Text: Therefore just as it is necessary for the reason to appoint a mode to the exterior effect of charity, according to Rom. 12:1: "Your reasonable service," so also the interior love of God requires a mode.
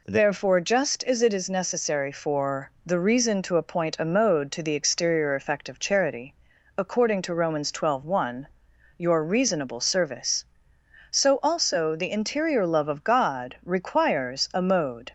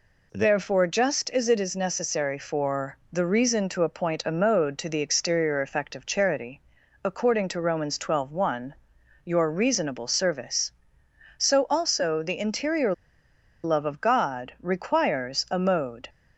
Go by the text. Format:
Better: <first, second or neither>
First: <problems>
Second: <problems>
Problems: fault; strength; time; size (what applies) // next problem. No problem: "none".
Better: first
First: none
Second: pauses between "interior" and "love"; noticeable; at 12.9 s; 0.70 s long